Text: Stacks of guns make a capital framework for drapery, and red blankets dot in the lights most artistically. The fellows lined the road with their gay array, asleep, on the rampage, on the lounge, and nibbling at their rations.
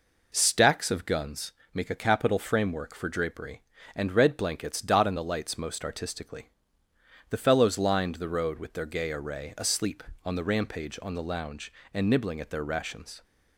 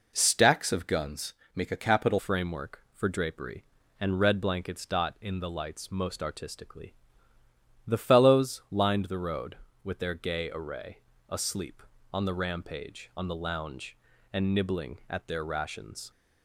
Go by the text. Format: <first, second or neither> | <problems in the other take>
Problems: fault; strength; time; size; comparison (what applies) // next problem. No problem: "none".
first | pauses between "guns" and "make"; slight; at 1.3 s; 0.22 s long; slight in the first // changes voice at "framework"; from 2.1 s on; 14.0 s long